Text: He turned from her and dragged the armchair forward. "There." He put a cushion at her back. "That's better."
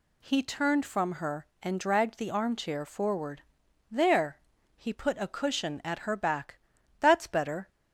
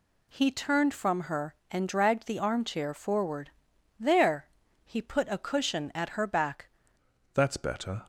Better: first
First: none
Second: changes voice at "That's"; from 7.3 s on; 0.7 s long

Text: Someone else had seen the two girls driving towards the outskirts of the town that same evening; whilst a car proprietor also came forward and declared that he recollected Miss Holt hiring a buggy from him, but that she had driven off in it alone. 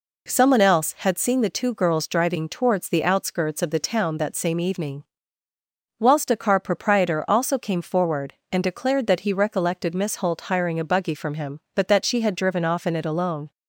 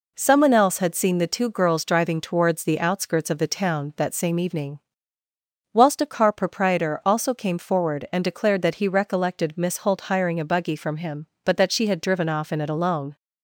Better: neither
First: none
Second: none

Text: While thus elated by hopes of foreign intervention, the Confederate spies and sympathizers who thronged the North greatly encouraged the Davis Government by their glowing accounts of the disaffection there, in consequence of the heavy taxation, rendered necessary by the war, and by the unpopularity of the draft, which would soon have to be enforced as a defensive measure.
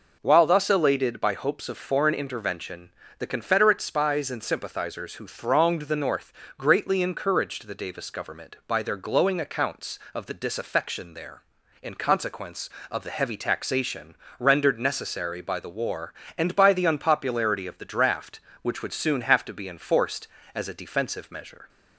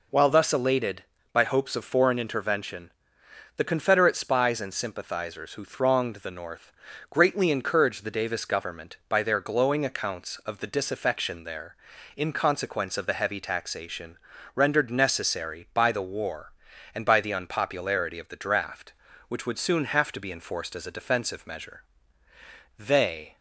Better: first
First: pauses between "North" and "greatly"; slight; at 6.3 s; 0.26 s long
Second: pauses between "North" and "greatly"; at 6.7 s; 0.38 s long // goes on to say "They"; from 22.7 s on; 0.58 s long

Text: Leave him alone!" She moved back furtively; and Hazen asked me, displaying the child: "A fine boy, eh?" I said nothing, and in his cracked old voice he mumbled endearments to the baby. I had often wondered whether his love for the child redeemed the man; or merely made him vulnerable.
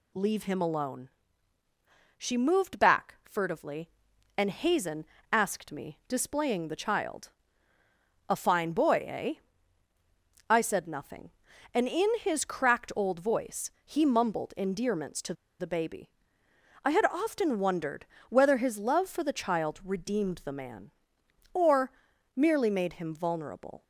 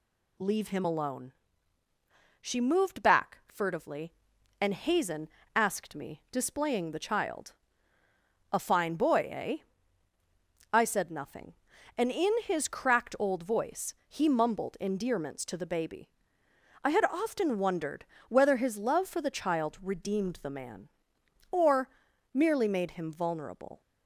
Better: second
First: pauses between "Hazen" and "asked"; slight; at 5.0 s; 0.26 s long // pauses between "voice" and "he"; slight; at 13.7 s; 0.16 s long // pauses between "to" and "the"; slight; at 15.3 s; 0.26 s long // pauses between "wondered" and "whether"; slight; at 18.0 s; 0.24 s long // pauses between "or" and "merely"; at 21.9 s; 0.44 s long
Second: pauses between "Hazen" and "asked"; slight; at 5.2 s; 0.26 s long // pauses between "voice" and "he"; slight; at 13.9 s; 0.16 s long // pauses between "wondered" and "whether"; slight; at 18.0 s; 0.24 s long // pauses between "or" and "merely"; at 21.8 s; 0.44 s long

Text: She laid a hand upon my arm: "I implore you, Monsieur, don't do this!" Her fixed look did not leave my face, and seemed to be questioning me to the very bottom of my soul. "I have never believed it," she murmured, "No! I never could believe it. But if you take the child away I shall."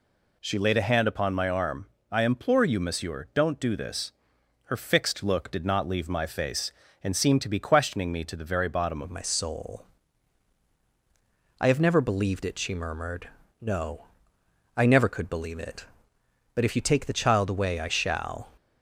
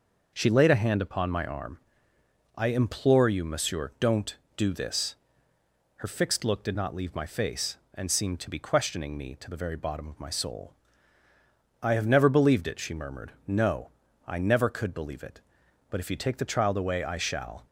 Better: second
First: changes voice at "of"; from 9.0 s on; 9.5 s long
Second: none

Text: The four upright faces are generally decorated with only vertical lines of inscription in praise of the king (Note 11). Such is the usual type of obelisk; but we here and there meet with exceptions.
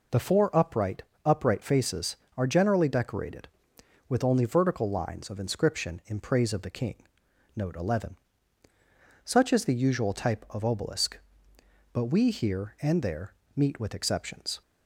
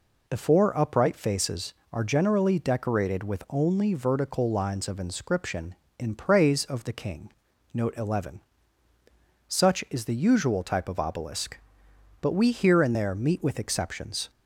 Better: second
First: says "upright" twice; at 1.2 s // pauses between "there" and "meet"; slight; at 13.3 s; 0.18 s long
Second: none

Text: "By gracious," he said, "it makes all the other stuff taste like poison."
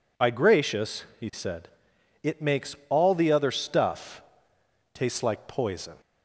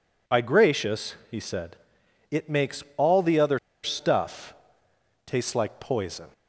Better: first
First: pauses between "stuff" and "taste"; noticeable; at 4.2 s; 0.72 s long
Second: pauses between "other" and "stuff"; slight; at 3.5 s; 0.25 s long // pauses between "stuff" and "taste"; noticeable; at 4.5 s; 0.72 s long

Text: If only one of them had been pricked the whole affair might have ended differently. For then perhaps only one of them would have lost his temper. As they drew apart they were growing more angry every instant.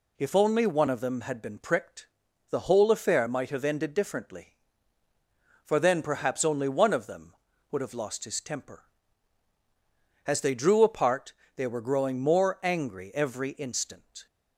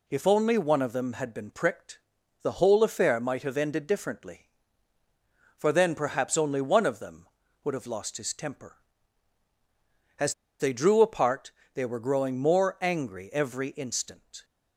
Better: first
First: pauses between "pricked" and "the"; at 2.0 s; 0.44 s long // pauses between "apart" and "they"; slight; at 11.3 s; 0.24 s long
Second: pauses between "pricked" and "the"; at 1.9 s; 0.44 s long // pauses between "As" and "they"; slight; at 10.3 s; 0.26 s long // pauses between "apart" and "they"; slight; at 11.5 s; 0.24 s long

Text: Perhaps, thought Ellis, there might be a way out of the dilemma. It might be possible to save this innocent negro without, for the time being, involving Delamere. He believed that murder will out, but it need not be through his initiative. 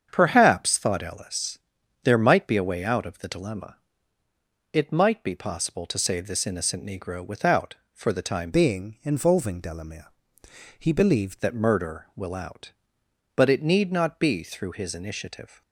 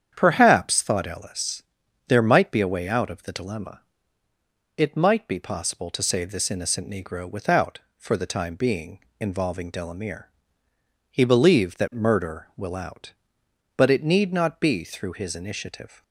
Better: second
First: starts louder than the rest; strong; until 1.1 s; 7.5 dB // changes voice from "being" to "believed"; from 8.5 to 11.4 s; 2.9 s long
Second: starts louder than the rest; strong; until 1.1 s; 8.5 dB

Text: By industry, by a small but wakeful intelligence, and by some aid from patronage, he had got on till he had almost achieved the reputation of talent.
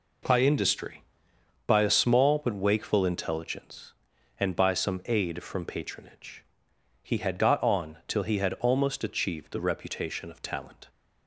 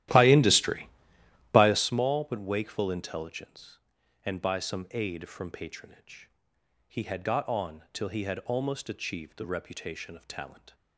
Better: first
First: none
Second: starts louder than the rest; strong; until 1.8 s; 13.5 dB

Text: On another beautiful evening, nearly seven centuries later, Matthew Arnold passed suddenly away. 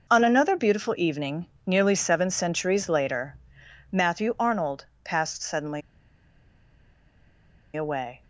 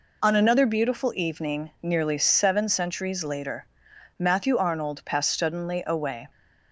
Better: second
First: pauses between "Arnold" and "passed"; slight; at 4.8 s; 0.18 s long // pauses between "suddenly" and "away"; strong; at 5.8 s; 1.9 s long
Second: none

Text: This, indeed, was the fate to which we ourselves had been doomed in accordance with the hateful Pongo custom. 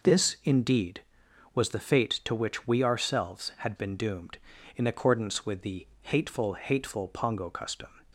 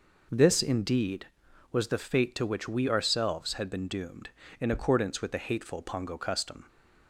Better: second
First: pauses between "the" and "hateful"; slight; at 5.8 s; 0.16 s long // says "hateful" twice; at 6.5 s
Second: none

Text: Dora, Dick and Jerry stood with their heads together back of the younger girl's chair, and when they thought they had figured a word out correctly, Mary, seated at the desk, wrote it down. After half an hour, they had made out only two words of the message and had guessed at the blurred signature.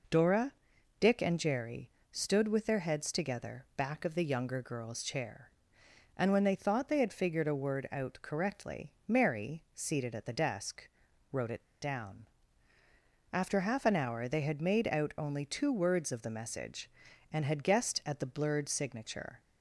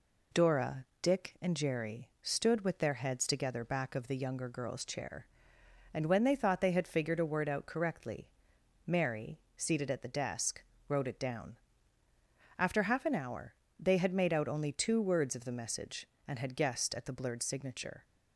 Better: second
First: pauses between "Jerry" and "stood"; slight; at 1.8 s; 0.22 s long // pauses between "it" and "down"; slight; at 11.6 s; 0.20 s long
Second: none

